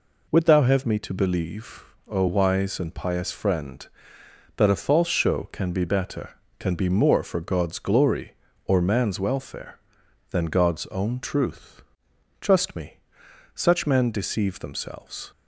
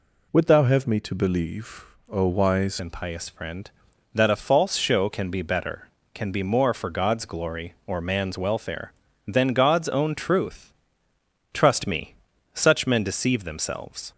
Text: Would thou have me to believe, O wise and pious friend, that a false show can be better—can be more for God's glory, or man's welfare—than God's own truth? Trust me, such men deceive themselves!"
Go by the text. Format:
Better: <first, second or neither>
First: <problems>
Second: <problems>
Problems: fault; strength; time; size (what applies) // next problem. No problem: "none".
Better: first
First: none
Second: changes voice at "and"; from 2.7 s on; 11.4 s long